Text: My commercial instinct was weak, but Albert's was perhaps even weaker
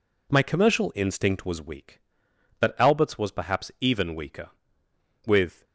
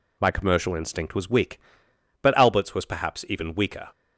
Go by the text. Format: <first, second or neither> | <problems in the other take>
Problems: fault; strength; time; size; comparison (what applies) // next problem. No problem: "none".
second | goes on to say "With"; slight; from 5.2 s on; 0.38 s long